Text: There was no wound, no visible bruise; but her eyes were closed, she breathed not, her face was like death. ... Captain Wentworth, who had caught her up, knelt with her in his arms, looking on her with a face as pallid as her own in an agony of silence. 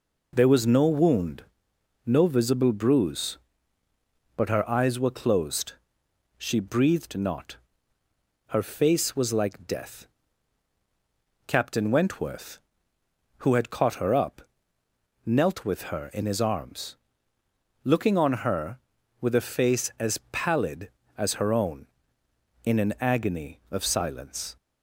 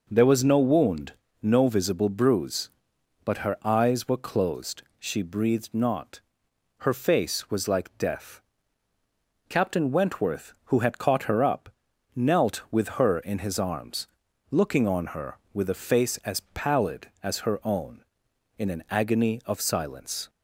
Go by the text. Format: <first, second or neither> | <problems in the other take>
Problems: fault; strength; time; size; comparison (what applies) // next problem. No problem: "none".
neither | none